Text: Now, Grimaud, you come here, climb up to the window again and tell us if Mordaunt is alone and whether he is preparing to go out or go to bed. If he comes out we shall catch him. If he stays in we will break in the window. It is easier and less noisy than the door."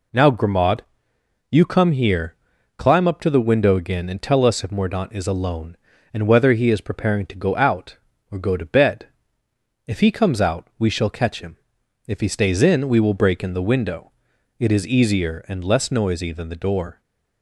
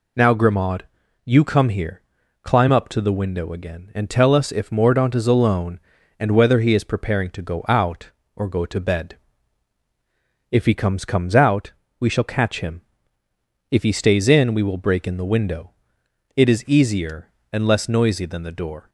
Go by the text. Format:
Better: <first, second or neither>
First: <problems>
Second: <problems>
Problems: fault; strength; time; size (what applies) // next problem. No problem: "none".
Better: first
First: none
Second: says "comes" twice; at 11.0 s // pauses between "out" and "we"; slight; at 11.7 s; 0.26 s long